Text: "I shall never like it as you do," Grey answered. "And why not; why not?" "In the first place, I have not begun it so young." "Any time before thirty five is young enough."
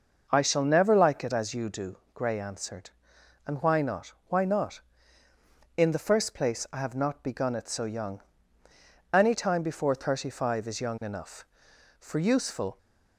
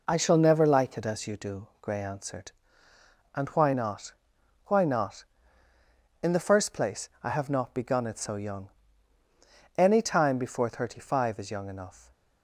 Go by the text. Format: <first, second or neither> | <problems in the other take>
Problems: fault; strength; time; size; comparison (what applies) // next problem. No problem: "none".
second | goes on to say "For useful"; noticeable; from 11.9 s on; 0.78 s long